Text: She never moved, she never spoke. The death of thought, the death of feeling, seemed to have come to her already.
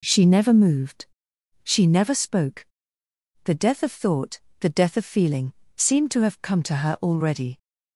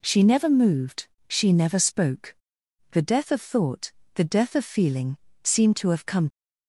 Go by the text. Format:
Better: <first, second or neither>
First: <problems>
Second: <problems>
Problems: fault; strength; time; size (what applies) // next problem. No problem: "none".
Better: first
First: none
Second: stops before "to her already"; at 6.3 s